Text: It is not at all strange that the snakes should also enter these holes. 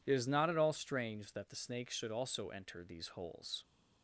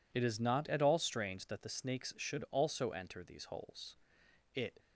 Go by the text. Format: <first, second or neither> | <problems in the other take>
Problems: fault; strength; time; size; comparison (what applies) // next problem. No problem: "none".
first | goes on to say "It"; slight; from 4.5 s on; 0.24 s long